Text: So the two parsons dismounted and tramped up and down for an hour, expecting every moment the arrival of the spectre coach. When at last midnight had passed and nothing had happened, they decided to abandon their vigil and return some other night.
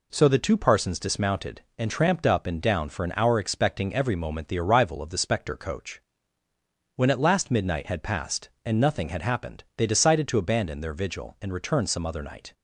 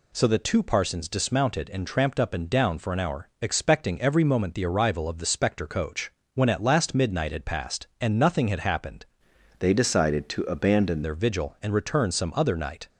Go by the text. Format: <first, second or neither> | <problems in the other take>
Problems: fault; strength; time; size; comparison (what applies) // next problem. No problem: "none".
first | changes voice from "they" to "abandon"; from 9.5 to 11.0 s; 1.5 s long